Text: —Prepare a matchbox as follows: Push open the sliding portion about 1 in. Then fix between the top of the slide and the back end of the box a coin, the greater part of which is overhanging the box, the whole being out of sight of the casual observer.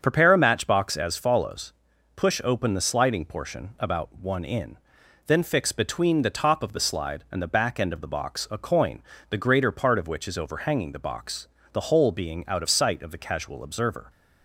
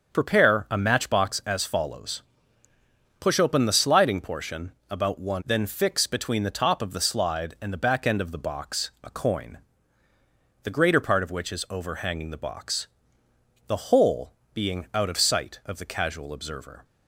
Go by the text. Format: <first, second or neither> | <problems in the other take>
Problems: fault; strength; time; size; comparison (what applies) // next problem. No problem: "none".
first | starts louder than the rest; until 1.1 s; 6.5 dB; strong in the first // pauses between "portion" and "about"; slight; at 4.7 s; 0.16 s long // skips "in"; at 5.4 s // pauses between "whole" and "being"; slight; at 14.3 s; 0.18 s long